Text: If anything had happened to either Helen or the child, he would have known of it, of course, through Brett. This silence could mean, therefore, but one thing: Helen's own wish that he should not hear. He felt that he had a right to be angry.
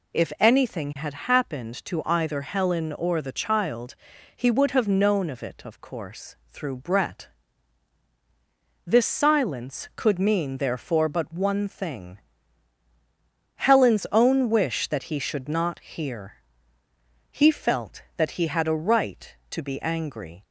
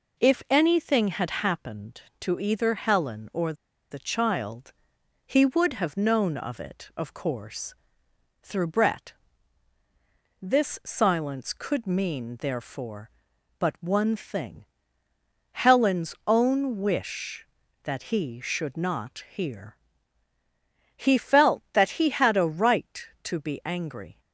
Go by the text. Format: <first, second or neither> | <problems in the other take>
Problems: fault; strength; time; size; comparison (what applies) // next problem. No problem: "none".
first | pauses between "or" and "the"; at 3.5 s; 0.37 s long